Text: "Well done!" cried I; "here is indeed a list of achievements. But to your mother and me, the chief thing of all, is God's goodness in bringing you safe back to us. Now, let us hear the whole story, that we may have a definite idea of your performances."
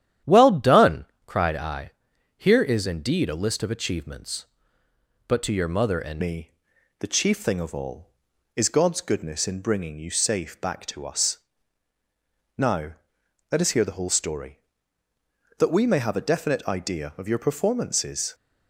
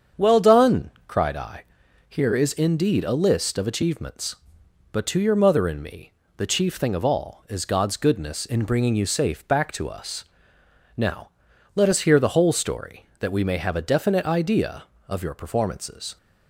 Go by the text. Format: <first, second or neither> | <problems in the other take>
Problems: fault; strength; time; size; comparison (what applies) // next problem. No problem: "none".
second | starts louder than the rest; strong; until 1.4 s; 10.5 dB; strong in the second // changes voice at "me"; from 6.2 s on; 12.1 s long